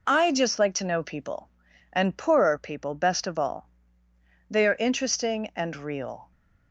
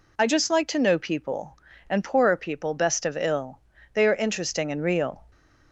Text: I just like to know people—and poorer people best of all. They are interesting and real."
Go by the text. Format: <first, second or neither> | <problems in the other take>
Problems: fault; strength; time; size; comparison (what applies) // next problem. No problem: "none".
first | says "ill" for "all"; at 3.1 s